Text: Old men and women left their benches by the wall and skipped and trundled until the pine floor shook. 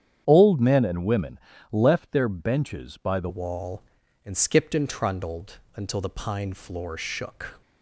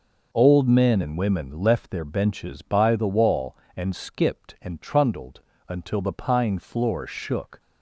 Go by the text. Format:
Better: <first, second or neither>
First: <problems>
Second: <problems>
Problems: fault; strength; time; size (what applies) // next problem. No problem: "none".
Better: second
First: starts louder than the rest; strong; until 1.2 s; 9 dB // pauses between "women" and "left"; slight; at 1.3 s; 0.32 s long // changes voice at "wall"; from 3.2 s on; 4.4 s long // pauses between "trundled" and "until"; slight; at 5.5 s; 0.18 s long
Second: pauses between "trundled" and "until"; slight; at 5.3 s; 0.28 s long